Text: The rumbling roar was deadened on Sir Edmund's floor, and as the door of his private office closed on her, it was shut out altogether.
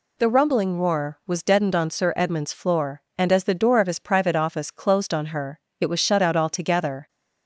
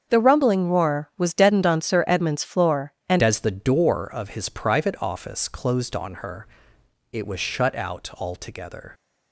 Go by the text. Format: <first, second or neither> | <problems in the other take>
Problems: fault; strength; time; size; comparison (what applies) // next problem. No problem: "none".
first | starts louder than the rest; strong; until 1.1 s; 7 dB // changes voice at "as"; from 3.1 s on; 5.8 s long